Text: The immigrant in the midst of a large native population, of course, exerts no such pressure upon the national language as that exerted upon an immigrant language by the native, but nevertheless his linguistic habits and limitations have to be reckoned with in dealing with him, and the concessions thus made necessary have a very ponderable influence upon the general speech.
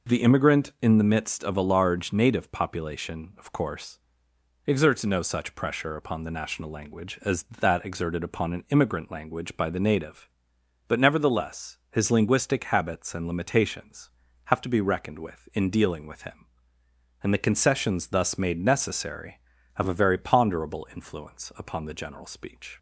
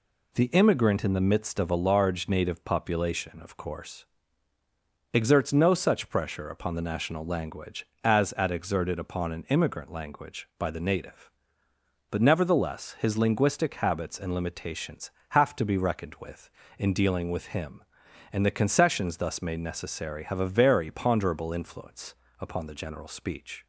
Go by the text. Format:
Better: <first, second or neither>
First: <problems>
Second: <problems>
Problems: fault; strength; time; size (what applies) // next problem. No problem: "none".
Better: first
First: none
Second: says "at" for "that"; at 8.3 s // pauses between "influence" and "upon"; slight; at 22.1 s; 0.24 s long